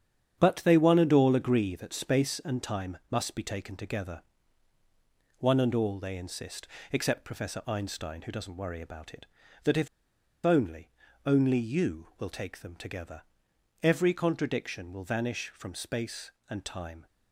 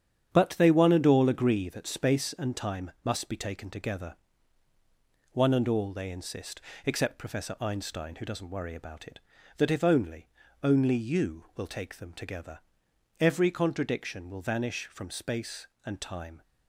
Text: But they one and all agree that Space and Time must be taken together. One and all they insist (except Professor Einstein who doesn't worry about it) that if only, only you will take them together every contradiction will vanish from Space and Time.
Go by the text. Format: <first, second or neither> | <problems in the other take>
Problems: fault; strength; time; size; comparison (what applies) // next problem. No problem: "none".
second | starts louder than the rest; strong; until 1.4 s; 8.5 dB; strong in the second // pauses between "if" and "only"; noticeable; at 9.8 s; 0.58 s long // pauses between "together" and "every"; noticeable; at 13.2 s; 0.60 s long; noticeable in the second